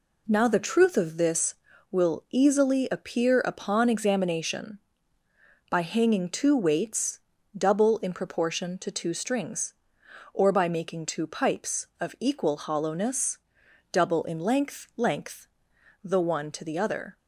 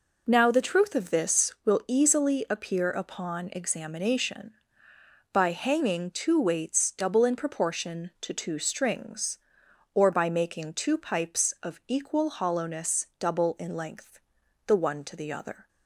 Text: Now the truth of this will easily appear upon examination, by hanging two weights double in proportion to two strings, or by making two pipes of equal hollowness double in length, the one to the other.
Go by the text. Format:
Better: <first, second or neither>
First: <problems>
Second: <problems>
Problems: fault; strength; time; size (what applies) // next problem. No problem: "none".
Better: second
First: pauses between "weights" and "double"; slight; at 7.1 s; 0.36 s long // pauses between "hollowness" and "double"; noticeable; at 13.3 s; 0.54 s long // says "length" twice; at 14.9 s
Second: none